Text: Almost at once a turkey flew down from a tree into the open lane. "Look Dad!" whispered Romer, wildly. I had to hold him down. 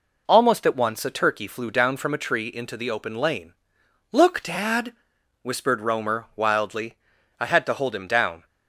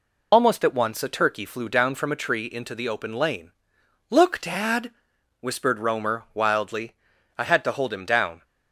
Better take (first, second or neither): first